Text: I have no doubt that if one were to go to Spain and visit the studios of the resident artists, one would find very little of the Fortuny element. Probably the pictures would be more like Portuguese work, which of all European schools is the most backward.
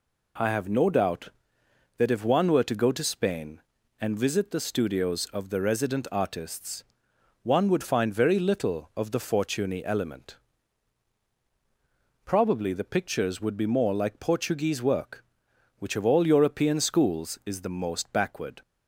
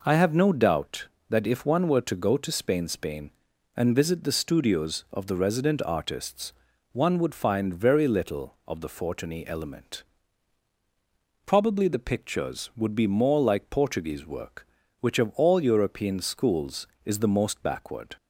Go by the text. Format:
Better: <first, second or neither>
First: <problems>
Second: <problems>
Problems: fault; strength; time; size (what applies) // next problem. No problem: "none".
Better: first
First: none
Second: says "Spain" twice; at 2.8 s